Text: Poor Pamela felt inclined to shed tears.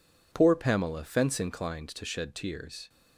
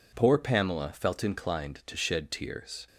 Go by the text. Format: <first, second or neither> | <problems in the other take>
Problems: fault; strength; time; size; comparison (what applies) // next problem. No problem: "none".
second | says "fence" for "felt"; at 1.0 s